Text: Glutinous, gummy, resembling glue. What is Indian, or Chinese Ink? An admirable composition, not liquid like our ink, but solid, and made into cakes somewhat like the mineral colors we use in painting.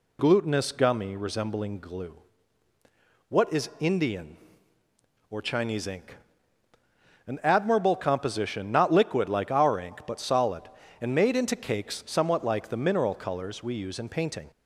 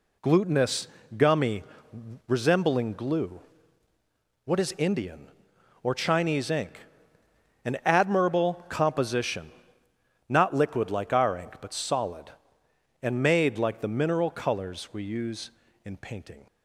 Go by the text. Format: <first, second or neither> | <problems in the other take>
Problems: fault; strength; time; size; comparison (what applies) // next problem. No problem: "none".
first | skips "into cakes somewhat"; at 13.5 s